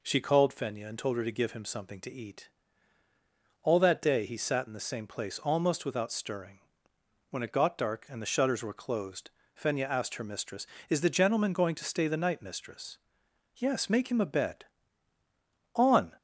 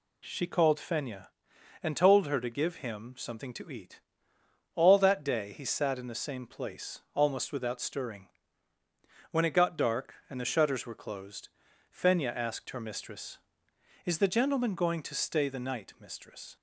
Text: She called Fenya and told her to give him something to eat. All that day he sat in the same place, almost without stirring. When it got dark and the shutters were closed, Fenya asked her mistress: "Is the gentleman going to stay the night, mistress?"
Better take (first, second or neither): second